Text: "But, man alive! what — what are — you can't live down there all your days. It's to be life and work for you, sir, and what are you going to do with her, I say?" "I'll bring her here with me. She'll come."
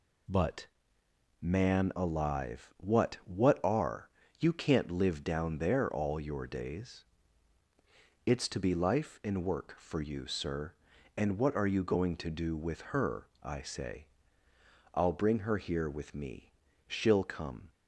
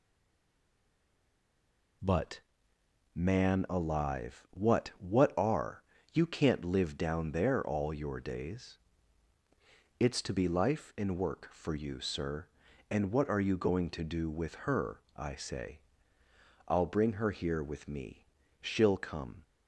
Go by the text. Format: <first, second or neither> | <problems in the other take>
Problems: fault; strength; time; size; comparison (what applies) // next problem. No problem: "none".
first | stays silent before the first word; noticeable; until 2.0 s; 2.0 s long